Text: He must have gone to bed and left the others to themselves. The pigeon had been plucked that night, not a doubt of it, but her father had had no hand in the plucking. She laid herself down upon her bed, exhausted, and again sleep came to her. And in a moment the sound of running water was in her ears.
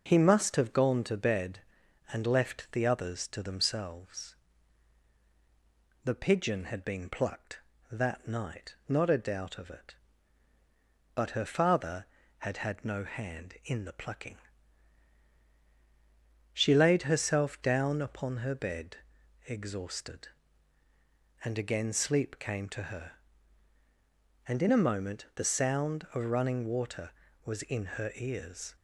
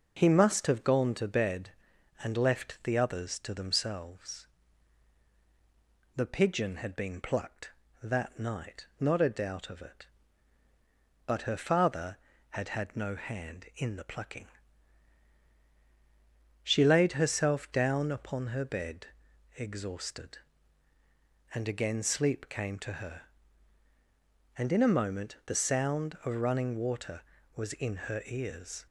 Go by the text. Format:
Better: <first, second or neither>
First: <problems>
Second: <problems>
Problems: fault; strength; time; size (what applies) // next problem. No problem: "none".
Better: neither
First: none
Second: none